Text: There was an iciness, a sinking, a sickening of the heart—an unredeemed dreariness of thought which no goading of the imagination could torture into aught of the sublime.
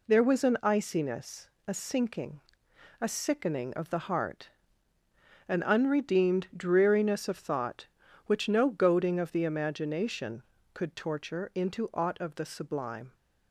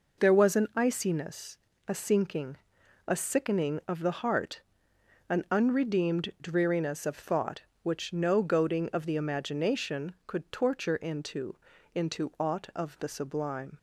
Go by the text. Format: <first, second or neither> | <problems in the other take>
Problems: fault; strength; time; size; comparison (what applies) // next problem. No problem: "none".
first | says "into" twice; at 11.9 s